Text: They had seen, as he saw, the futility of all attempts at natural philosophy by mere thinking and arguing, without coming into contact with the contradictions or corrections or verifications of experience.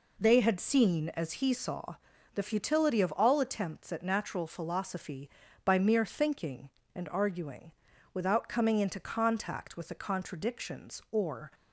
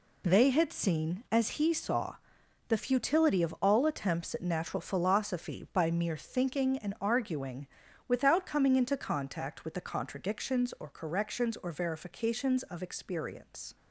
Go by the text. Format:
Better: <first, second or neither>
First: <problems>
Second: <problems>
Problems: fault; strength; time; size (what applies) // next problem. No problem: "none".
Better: second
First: stops before "corrections or verifications of experience"; at 11.5 s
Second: none